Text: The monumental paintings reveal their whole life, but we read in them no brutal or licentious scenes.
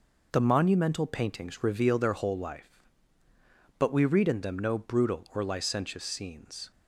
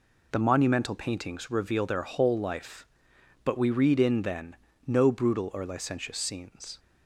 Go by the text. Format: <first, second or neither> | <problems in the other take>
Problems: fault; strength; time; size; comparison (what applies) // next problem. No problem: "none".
first | says "then" for "them"; at 4.2 s